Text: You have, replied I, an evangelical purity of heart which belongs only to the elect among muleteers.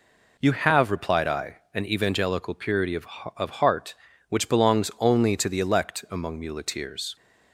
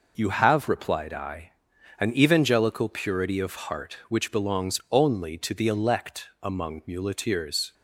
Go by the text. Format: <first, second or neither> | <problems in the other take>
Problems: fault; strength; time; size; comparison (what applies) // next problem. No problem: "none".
second | says "of" twice; at 3.3 s